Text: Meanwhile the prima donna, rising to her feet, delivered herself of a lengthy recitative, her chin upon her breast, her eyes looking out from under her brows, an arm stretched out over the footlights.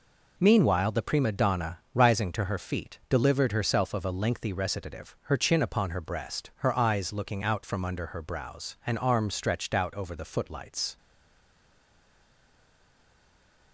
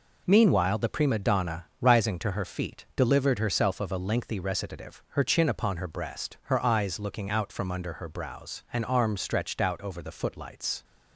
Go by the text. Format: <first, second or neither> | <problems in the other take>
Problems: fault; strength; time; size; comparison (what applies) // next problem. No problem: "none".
second | stays silent after the last word; strong; from 10.9 s on; 2.8 s long